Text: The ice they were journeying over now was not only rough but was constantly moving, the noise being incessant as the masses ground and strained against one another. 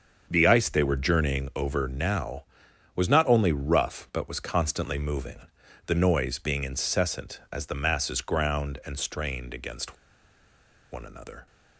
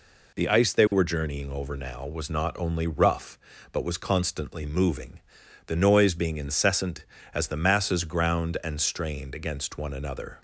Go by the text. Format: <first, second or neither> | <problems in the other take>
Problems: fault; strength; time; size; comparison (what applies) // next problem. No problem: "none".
second | starts louder than the rest; until 1.3 s; 7 dB // pauses between "against" and "one"; noticeable; at 9.9 s; 0.96 s long